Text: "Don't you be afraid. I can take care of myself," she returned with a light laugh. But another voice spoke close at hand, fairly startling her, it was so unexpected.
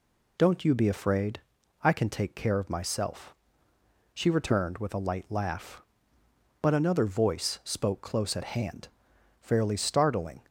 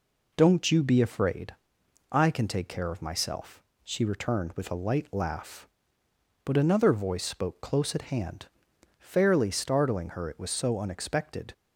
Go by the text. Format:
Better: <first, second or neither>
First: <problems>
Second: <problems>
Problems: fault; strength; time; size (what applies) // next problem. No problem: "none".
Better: second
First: stops before "her it was so unexpected"; at 10.4 s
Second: none